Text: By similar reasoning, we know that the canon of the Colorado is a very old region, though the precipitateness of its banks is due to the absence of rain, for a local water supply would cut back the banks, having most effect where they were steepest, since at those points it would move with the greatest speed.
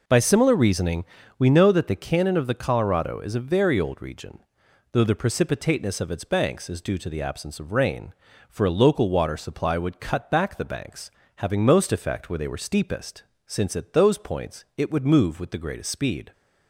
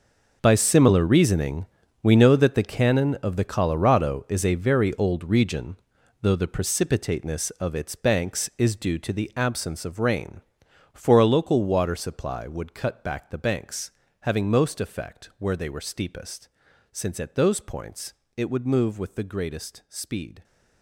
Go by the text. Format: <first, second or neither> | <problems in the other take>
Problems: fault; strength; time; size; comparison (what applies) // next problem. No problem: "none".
first | gets quieter; strong; throughout; 14 dB // pauses between "points" and "it"; slight; at 18.1 s; 0.22 s long